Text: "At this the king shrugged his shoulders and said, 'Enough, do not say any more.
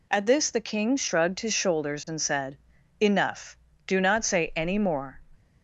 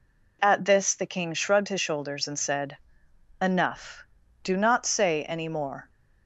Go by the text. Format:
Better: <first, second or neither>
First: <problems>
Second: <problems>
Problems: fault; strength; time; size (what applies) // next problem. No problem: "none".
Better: neither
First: none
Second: none